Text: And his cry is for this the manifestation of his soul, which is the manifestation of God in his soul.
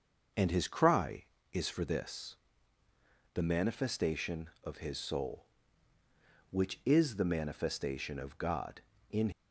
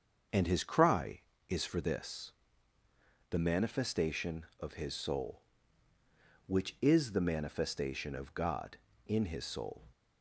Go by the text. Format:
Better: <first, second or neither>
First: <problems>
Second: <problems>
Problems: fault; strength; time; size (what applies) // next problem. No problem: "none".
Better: second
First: starts louder than the rest; noticeable; until 1.6 s; 6 dB // pauses between "this" and "the"; noticeable; at 2.3 s; 0.98 s long // stops before "his soul"; at 9.3 s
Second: starts louder than the rest; until 1.5 s; 6.5 dB // pauses between "this" and "the"; noticeable; at 2.3 s; 0.98 s long